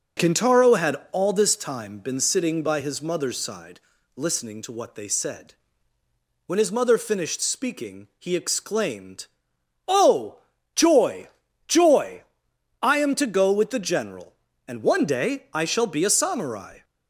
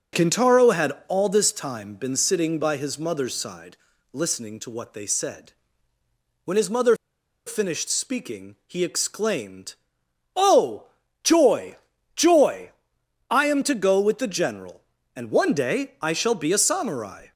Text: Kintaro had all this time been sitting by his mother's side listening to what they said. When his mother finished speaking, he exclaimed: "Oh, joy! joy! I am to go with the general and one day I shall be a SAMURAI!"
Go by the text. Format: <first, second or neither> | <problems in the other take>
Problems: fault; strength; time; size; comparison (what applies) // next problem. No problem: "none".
first | pauses between "had" and "all"; slight; at 0.9 s; 0.16 s long; slight in the first // pauses between "side" and "listening"; slight; at 3.7 s; 0.36 s long; slight in the first // pauses between "mother" and "finished"; noticeable; at 6.9 s; 0.52 s long